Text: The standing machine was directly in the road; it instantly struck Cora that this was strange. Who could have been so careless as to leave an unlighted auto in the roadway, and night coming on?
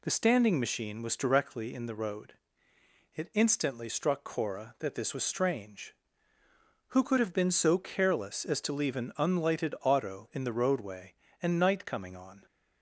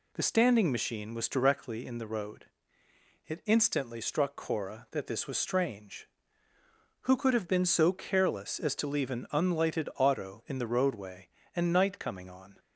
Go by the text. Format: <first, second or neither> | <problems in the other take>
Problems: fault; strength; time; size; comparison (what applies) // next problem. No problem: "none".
neither | none